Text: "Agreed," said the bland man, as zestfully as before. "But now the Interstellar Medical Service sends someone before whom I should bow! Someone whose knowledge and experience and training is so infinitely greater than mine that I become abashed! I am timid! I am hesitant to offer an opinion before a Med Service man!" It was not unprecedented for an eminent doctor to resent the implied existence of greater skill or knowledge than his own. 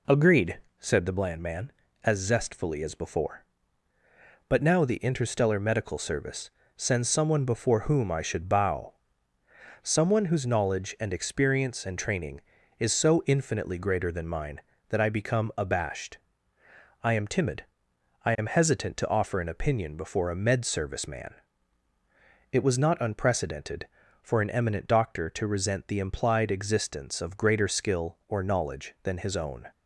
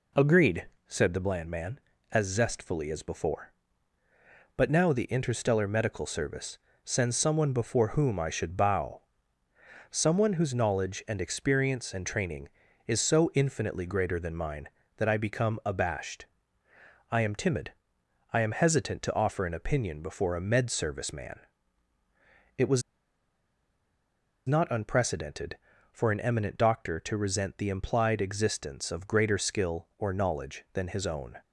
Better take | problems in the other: first | pauses between "Service" and "sends"; slight; at 6.5 s; 0.26 s long; slight in the first // pauses between "was" and "not"; strong; at 22.8 s; 1.6 s long

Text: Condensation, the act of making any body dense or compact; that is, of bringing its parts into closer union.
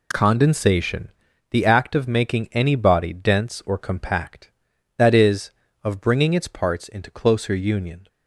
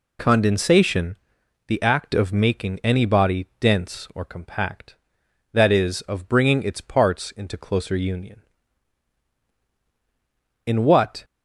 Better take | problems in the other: first | goes on to say "In what"; from 10.6 s on; 0.58 s long

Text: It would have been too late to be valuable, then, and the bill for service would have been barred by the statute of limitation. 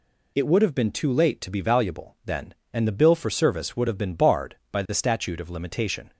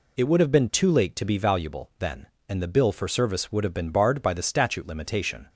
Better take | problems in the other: first | skips "of"; at 4.8 s

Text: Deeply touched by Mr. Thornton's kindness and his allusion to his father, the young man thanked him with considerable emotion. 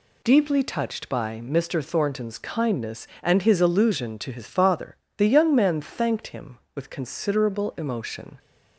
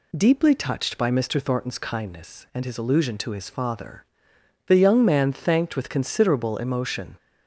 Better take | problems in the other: first | skips "him"; at 5.7 s

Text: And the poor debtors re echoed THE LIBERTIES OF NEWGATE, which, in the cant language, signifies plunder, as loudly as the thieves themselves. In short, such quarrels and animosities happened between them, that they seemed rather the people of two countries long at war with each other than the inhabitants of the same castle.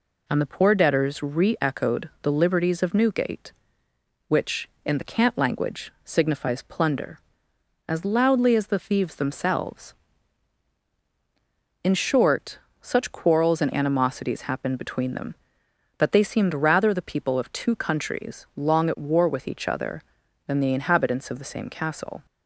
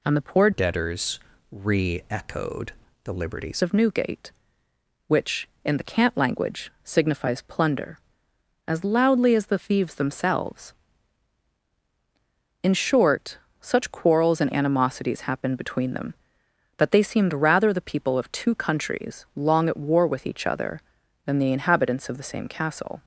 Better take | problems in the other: first | changes voice from "debtors" to "LIBERTIES"; from 0.5 to 3.6 s; 3.1 s long // pauses between "debtors" and "re"; slight; at 1.1 s; 0.32 s long // pauses between "echoed" and "THE"; slight; at 2.7 s; 0.32 s long

